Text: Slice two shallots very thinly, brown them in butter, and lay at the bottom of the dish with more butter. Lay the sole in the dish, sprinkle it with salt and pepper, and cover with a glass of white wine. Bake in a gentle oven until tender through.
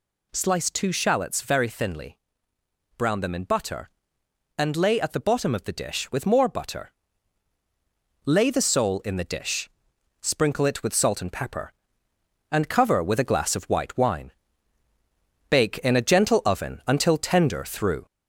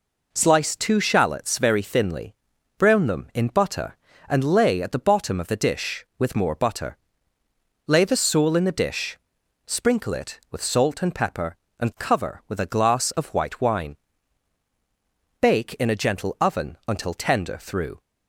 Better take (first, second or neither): second